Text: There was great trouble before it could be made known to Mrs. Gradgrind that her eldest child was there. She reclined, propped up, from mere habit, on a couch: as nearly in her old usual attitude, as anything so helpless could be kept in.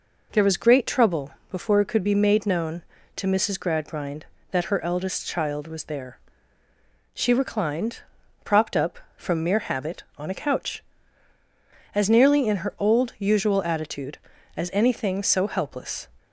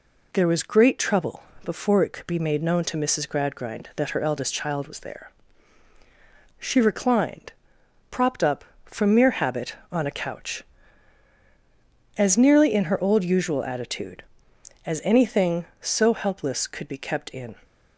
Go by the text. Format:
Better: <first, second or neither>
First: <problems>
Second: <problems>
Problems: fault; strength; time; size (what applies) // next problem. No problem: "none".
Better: second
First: pauses between "trouble" and "before"; slight; at 1.3 s; 0.20 s long // stops before "could be kept in"; at 16.1 s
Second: pauses between "trouble" and "before"; slight; at 1.4 s; 0.24 s long